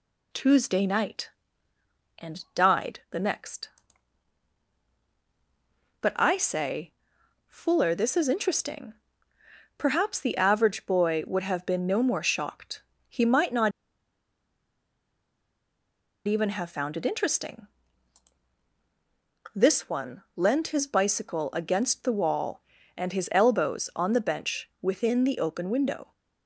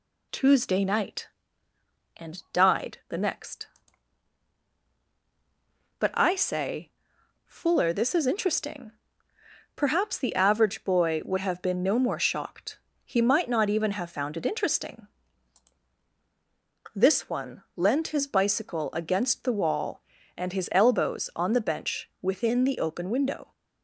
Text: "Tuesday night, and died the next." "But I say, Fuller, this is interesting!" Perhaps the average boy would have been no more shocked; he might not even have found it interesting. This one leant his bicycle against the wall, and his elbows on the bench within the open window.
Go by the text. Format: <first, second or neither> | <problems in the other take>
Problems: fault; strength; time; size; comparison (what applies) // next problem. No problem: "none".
second | pauses between "not" and "even"; strong; at 13.7 s; 2.5 s long